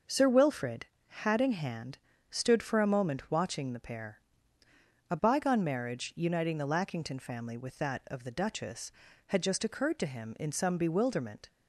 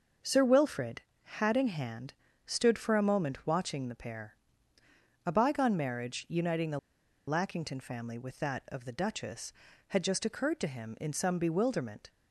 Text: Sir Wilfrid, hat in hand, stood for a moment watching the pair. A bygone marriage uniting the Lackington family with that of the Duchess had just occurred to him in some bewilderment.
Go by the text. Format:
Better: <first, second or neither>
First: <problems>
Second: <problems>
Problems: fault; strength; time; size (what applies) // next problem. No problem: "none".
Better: first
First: none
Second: pauses between "the" and "Lackington"; noticeable; at 6.7 s; 0.49 s long